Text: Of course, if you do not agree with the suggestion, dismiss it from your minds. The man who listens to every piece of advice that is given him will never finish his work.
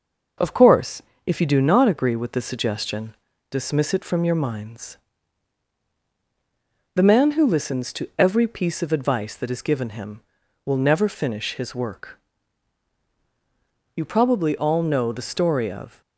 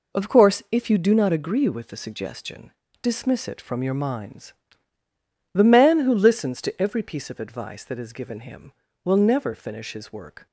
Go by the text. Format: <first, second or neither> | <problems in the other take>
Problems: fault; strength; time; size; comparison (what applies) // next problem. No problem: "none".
second | goes on to say "You probably all know the story of"; strong; from 13.9 s on; 2.0 s long